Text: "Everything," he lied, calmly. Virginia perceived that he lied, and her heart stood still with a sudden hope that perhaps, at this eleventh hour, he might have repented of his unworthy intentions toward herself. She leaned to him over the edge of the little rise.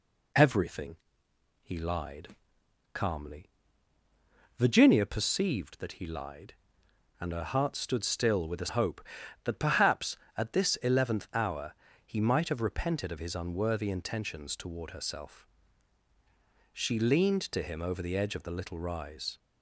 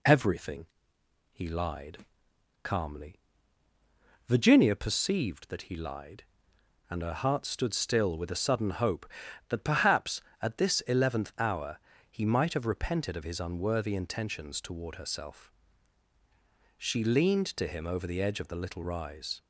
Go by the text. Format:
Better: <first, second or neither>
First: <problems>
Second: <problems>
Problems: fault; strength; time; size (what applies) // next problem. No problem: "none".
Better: second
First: skips "sudden"; at 8.6 s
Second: none